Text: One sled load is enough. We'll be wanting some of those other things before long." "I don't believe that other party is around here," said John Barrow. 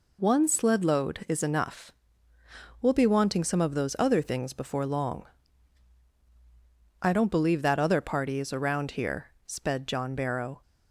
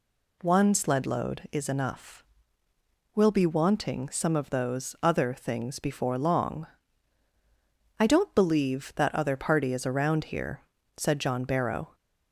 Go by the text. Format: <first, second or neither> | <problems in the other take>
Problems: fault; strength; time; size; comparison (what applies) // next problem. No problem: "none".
second | says "sped" for "said"; at 9.4 s